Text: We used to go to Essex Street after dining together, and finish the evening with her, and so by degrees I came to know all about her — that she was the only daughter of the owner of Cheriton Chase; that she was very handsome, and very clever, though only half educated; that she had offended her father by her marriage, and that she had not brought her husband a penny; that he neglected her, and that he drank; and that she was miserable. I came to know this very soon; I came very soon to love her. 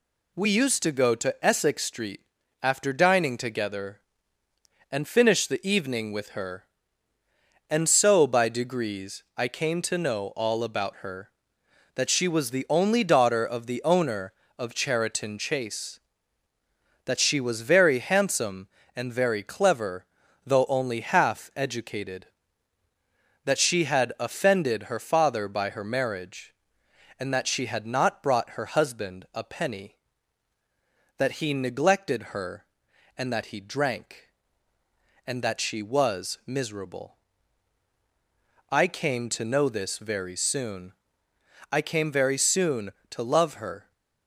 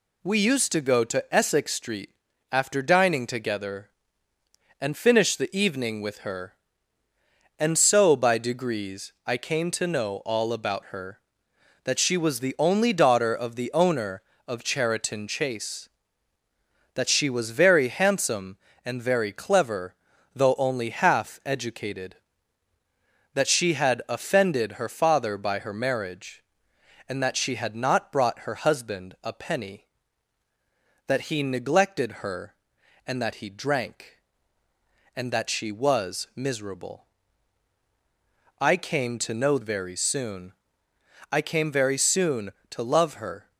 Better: first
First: pauses between "Street" and "after"; at 2.2 s; 0.40 s long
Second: pauses between "Street" and "after"; at 2.1 s; 0.40 s long // skips "this"; at 39.5 s

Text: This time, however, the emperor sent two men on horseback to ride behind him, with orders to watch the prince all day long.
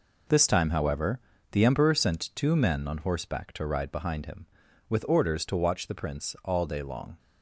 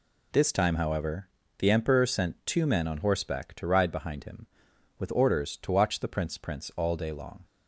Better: first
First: none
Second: says "prince" twice; at 6.3 s

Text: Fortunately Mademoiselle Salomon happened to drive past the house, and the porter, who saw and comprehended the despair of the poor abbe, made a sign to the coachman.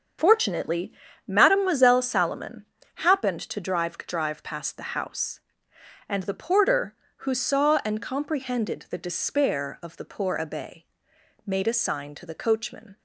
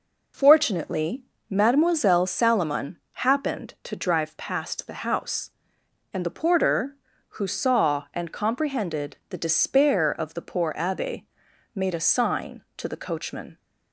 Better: second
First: starts louder than the rest; until 1.5 s; 7 dB // pauses between "Fortunately" and "Mademoiselle"; slight; at 0.9 s; 0.34 s long // pauses between "Salomon" and "happened"; slight; at 2.6 s; 0.30 s long // says "drive" twice; at 3.9 s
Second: pauses between "Fortunately" and "Mademoiselle"; slight; at 1.2 s; 0.26 s long // pauses between "Salomon" and "happened"; slight; at 2.9 s; 0.16 s long

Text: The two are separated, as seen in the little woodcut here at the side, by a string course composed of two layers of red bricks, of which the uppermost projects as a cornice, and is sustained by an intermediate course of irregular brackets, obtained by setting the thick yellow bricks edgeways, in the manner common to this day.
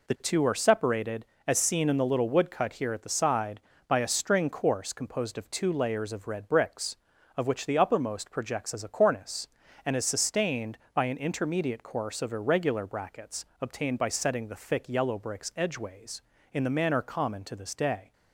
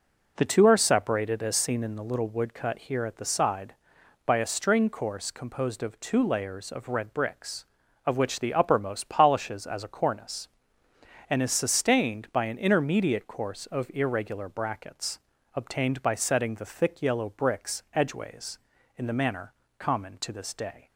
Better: first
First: none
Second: says "polishes" for "projects"; at 9.0 s // pauses between "manner" and "common"; slight; at 19.5 s; 0.26 s long

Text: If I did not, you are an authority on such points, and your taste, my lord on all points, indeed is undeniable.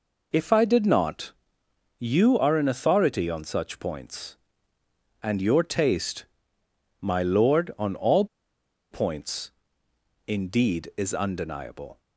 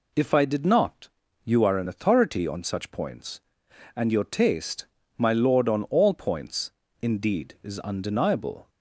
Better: second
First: pauses between "all" and "points"; noticeable; at 8.2 s; 0.66 s long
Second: none

